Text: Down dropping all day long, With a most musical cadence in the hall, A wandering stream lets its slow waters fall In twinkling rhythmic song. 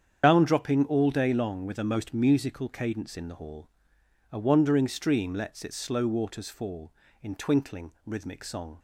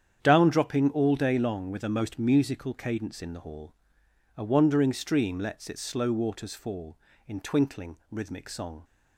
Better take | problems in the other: second | loses the start of "Down"; at 0.2 s; 65 ms // starts louder than the rest; strong; until 1.2 s; 8.5 dB; strong in the second

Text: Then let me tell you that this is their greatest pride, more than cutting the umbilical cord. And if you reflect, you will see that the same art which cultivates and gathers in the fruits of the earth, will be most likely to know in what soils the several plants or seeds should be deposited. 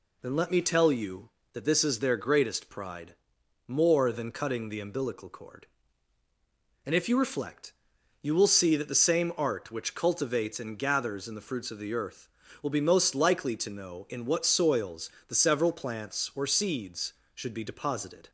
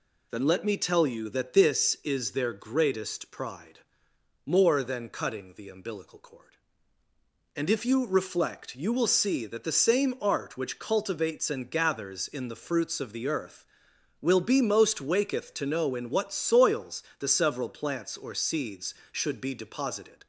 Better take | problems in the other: first | says "waketh" for "likely"; at 14.9 s // pauses between "soils" and "the"; slight; at 17.0 s; 0.16 s long; slight in the first

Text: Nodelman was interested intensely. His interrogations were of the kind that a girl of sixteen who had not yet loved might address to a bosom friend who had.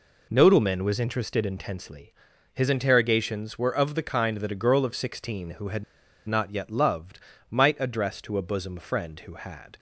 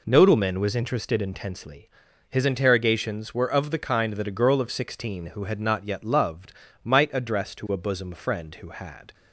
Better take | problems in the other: second | pauses between "had" and "not"; at 5.8 s; 0.42 s long // pauses between "loved" and "might"; slight; at 7.1 s; 0.32 s long; slight in the second

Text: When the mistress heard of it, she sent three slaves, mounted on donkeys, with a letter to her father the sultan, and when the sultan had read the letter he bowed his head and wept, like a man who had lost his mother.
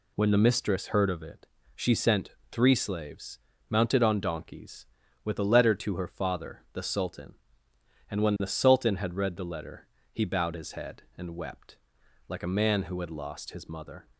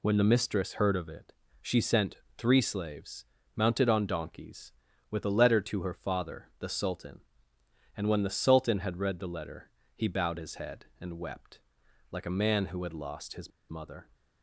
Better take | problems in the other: first | pauses between "sent" and "three"; slight; at 2.1 s; 0.20 s long; slight in the first // pauses between "letter" and "he"; slight; at 9.6 s; 0.24 s long; slight in the first // pauses between "his" and "mother"; slight; at 13.5 s; 0.19 s long

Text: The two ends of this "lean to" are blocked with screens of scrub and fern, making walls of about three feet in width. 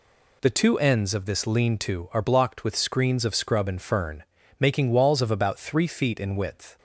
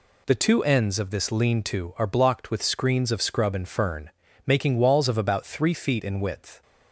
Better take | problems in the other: neither | none

